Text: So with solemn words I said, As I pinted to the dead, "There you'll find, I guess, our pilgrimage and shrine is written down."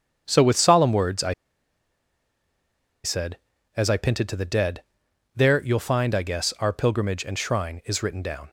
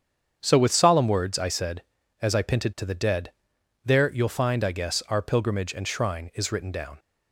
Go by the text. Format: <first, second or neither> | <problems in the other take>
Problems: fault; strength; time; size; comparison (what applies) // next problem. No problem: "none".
second | starts louder than the rest; strong; until 1.2 s; 7.5 dB; strong in the second // pauses between "I" and "said"; strong; at 1.3 s; 1.7 s long